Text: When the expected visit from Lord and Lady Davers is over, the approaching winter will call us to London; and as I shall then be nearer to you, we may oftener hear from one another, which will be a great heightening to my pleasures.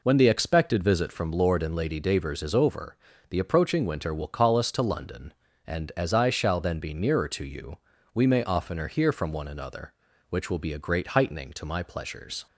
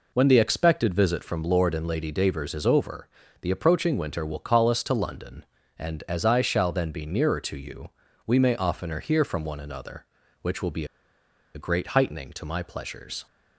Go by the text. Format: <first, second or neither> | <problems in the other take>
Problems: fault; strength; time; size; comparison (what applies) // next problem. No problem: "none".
first | pauses between "be" and "a"; noticeable; at 10.8 s; 0.70 s long